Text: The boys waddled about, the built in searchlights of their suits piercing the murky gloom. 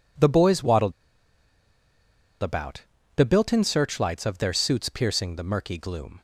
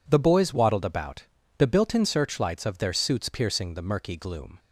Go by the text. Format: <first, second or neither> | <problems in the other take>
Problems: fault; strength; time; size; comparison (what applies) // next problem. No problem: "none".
second | pauses between "waddled" and "about"; strong; at 0.9 s; 1.4 s long